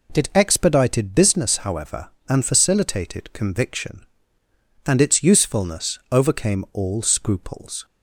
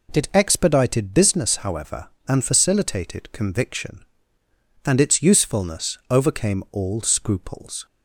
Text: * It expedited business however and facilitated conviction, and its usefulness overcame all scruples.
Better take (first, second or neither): neither